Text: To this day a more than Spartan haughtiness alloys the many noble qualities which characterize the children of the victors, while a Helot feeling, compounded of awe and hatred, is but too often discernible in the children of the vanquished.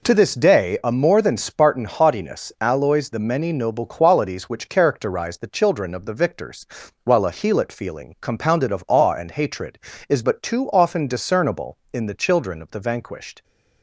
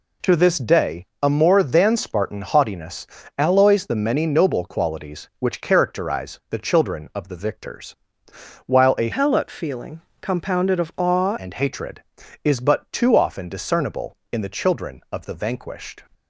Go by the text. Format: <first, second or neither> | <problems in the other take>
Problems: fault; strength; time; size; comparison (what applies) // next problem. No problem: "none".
first | pauses between "day" and "a"; slight; at 1.0 s; 0.16 s long // pauses between "haughtiness" and "alloys"; slight; at 3.0 s; 0.32 s long // changes voice from "Helot" to "awe"; from 9.1 to 11.3 s; 2.2 s long